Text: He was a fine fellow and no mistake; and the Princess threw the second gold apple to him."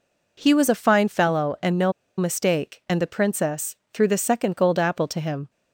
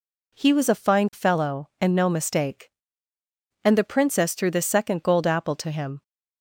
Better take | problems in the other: second | pauses between "no" and "mistake"; slight; at 1.9 s; 0.25 s long // pauses between "Princess" and "threw"; slight; at 3.7 s; 0.16 s long

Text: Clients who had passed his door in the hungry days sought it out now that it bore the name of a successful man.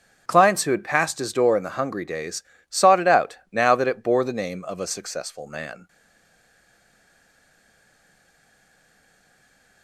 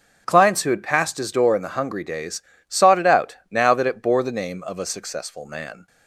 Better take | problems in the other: second | starts louder than the rest; until 1.2 s; 7 dB; also in the second // pauses between "days" and "sought"; slight; at 2.4 s; 0.26 s long; slight in the second // stays silent after the last word; strong; from 5.8 s on; 4.0 s long

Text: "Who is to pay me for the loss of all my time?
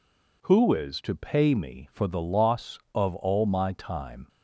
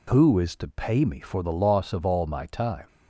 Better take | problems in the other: neither | none

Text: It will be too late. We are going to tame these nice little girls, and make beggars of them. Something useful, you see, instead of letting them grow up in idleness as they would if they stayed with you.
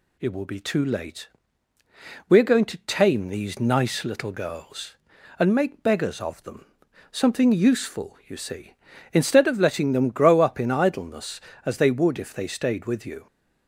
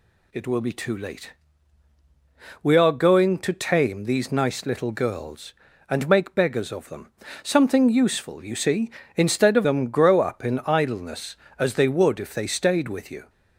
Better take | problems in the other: first | skips "letting"; at 9.6 s

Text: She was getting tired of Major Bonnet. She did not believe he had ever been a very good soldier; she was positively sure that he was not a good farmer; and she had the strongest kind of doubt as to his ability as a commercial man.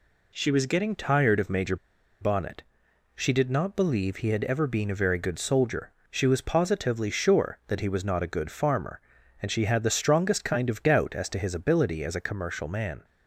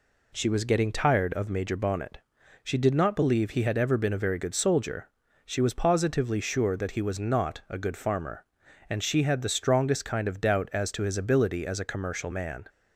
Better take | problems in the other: second | pauses between "Major" and "Bonnet"; at 1.7 s; 0.45 s long

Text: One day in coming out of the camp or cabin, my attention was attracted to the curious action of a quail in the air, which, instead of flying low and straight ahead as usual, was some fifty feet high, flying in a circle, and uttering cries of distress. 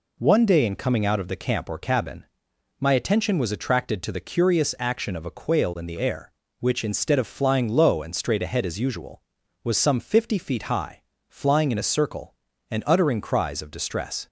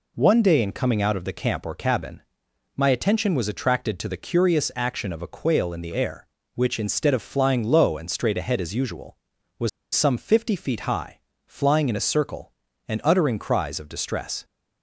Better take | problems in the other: first | pauses between "was" and "some"; slight; at 9.6 s; 0.24 s long

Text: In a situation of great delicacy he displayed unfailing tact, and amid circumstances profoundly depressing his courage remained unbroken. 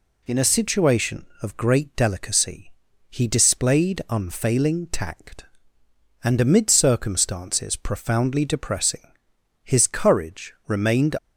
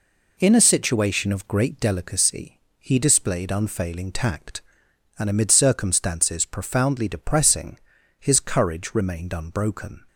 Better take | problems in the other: second | pauses between "delicacy" and "he"; at 2.7 s; 0.40 s long; slight in the second // pauses between "depressing" and "his"; noticeable; at 9.0 s; 0.64 s long; also in the second // stops before "unbroken"; at 11.1 s

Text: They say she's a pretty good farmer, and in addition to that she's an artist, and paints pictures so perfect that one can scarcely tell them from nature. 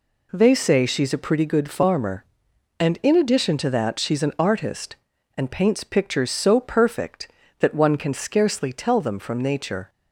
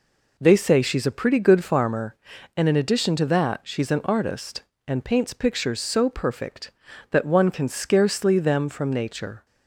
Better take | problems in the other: first | skips "tell"; at 8.3 s

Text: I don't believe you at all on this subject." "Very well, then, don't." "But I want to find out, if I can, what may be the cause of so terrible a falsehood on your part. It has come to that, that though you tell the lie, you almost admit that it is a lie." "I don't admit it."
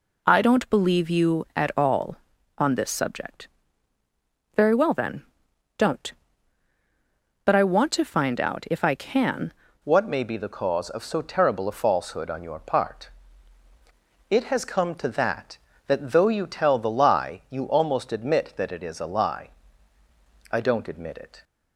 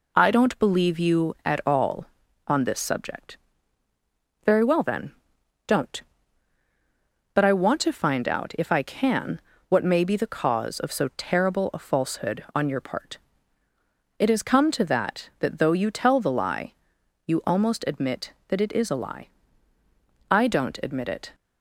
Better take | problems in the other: second | changes voice at "what"; from 9.8 s on; 11.6 s long

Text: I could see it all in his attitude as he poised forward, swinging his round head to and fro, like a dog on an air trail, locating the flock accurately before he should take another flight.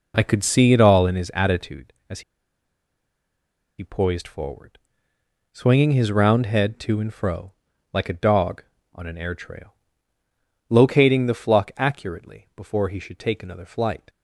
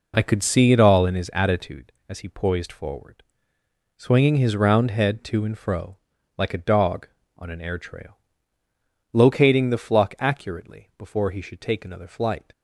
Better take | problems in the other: second | pauses between "as" and "he"; strong; at 2.2 s; 1.5 s long

